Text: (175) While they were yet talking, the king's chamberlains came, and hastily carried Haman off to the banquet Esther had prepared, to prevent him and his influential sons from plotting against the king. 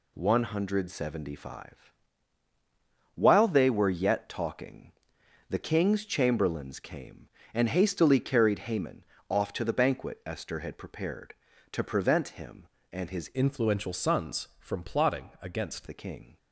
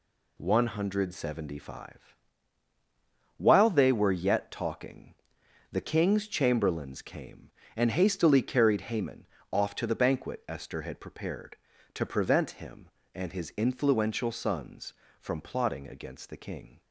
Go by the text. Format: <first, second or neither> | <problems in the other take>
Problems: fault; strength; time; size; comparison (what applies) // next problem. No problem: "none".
second | pauses between "Haman" and "off"; slight; at 9.0 s; 0.24 s long; slight in the second // changes voice from "influential" to "against"; from 13.3 to 15.8 s; 2.5 s long